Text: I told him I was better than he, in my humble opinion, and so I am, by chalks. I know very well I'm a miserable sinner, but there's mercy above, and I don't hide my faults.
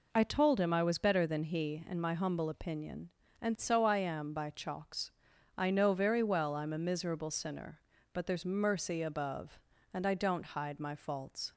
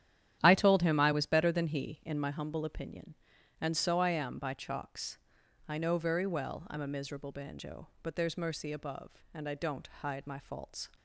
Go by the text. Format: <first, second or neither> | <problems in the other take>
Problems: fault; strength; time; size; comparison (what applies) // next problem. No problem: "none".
first | starts louder than the rest; strong; until 1.4 s; 10.5 dB // says "banjo" for "sinner"; at 7.3 s